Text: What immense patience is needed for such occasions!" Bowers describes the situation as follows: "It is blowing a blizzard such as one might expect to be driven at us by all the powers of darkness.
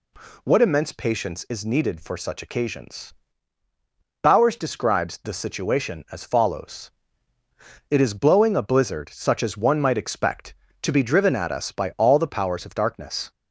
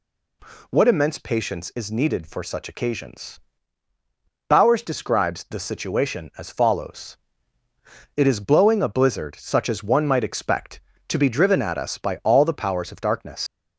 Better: first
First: none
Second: leaves "darkness" unfinished; at 13.4 s; 100 ms

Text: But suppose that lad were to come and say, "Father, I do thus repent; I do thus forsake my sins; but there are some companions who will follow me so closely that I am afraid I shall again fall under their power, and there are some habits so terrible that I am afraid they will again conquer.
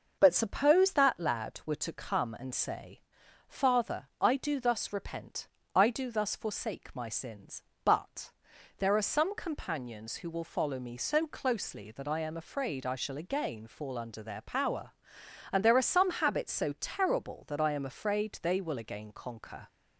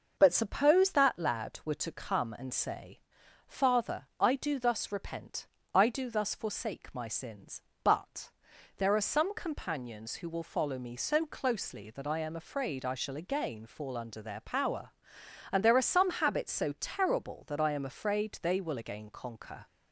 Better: neither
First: pauses between "but" and "there"; noticeable; at 8.3 s; 0.46 s long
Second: pauses between "but" and "there"; noticeable; at 8.3 s; 0.46 s long

